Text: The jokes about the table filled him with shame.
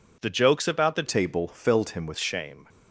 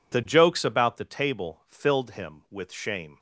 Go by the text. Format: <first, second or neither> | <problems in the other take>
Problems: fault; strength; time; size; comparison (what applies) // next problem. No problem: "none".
second | changes voice from "table" to "with"; from 1.0 to 2.1 s; 1.1 s long